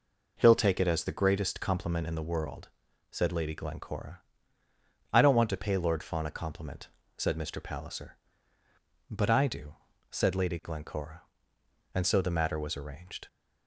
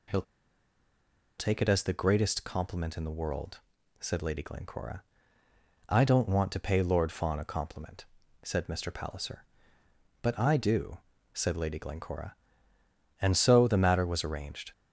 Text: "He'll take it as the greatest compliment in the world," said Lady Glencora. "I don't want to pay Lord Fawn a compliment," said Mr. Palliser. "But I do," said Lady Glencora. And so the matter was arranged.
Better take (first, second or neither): first